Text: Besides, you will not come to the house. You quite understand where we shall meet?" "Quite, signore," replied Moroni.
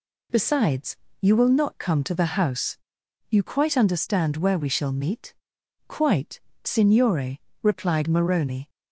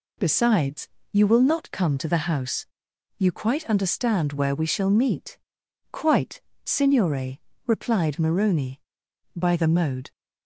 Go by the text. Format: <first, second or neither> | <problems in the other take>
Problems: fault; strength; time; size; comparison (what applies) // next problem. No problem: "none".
first | goes on to say "By the mode"; noticeable; from 9.3 s on; 0.74 s long